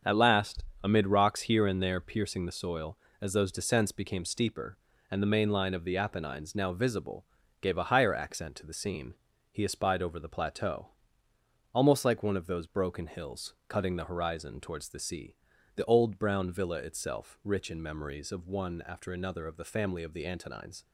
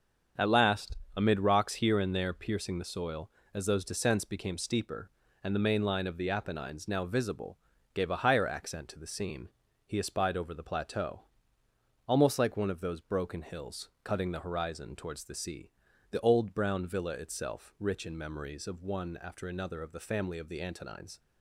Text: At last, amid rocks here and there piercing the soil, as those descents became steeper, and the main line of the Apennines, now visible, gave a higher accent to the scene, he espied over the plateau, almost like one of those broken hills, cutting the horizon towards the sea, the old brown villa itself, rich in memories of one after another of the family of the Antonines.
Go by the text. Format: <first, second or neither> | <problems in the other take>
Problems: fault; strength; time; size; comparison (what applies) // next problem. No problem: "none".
neither | starts louder than the rest; strong; the same in both